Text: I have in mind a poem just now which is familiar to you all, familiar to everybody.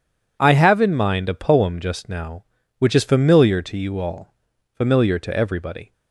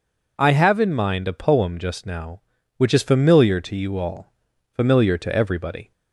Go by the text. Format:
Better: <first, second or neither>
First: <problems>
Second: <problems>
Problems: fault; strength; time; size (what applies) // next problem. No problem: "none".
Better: second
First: gets quieter; strong; throughout; 12.5 dB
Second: none